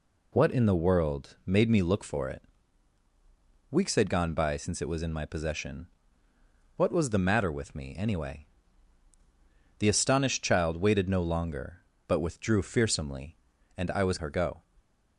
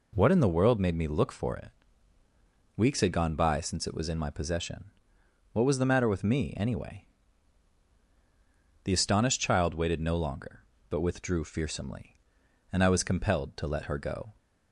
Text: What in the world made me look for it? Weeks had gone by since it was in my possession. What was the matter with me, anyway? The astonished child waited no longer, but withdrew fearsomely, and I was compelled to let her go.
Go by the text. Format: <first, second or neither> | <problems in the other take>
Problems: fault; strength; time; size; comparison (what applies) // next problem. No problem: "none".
second | skips "compelled to let"; at 14.1 s